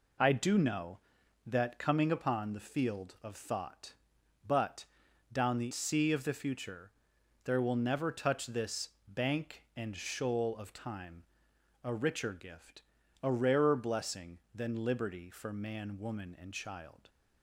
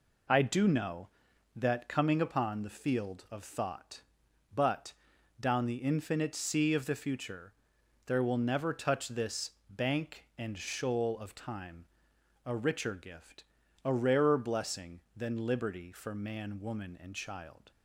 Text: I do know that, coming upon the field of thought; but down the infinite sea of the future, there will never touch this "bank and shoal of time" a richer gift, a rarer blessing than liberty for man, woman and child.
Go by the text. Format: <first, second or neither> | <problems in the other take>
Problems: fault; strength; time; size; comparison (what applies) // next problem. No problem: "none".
second | pauses between "but" and "down"; noticeable; at 4.8 s; 0.48 s long; noticeable in the second // skips "infinite"; at 5.7 s // pauses between "this" and "bank"; slight; at 8.8 s; 0.18 s long; slight in the second // pauses between "time" and "a"; noticeable; at 11.2 s; 0.60 s long; noticeable in the second